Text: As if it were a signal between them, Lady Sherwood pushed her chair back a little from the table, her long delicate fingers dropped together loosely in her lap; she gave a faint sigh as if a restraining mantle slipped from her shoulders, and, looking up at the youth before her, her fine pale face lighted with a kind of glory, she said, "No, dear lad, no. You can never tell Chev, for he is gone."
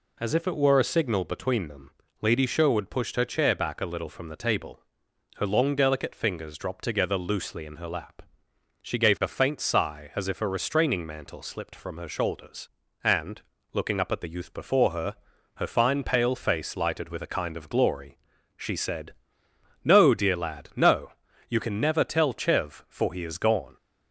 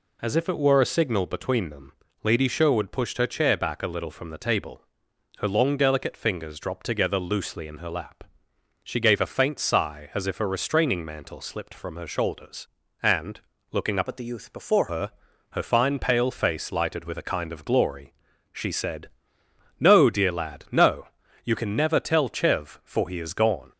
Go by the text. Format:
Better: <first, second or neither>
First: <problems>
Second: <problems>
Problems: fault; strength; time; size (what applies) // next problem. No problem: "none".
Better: first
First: none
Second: changes voice from "at" to "before"; from 14.0 to 14.8 s; 0.8 s long